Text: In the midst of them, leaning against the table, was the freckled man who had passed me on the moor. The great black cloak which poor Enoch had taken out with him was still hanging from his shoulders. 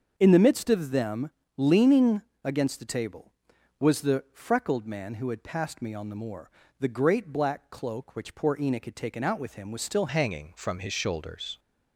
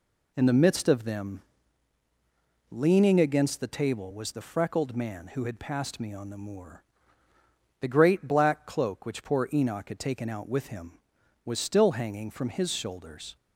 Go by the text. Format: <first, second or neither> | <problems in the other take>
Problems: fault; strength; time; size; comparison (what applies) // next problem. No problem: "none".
second | starts louder than the rest; until 1.1 s; 6.5 dB // pauses between "leaning" and "against"; slight; at 2.2 s; 0.24 s long // changes voice at "hanging"; from 10.0 s on; 1.5 s long